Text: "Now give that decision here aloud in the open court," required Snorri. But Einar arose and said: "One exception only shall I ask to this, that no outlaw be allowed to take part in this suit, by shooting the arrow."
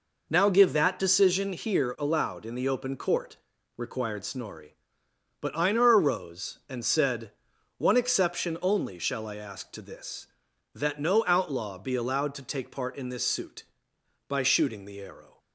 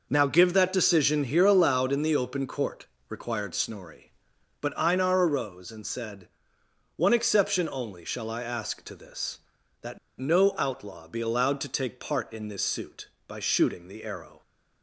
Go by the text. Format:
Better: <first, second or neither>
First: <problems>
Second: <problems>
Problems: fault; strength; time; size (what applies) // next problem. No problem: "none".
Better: first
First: none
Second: pauses between "that" and "no"; slight; at 9.9 s; 0.21 s long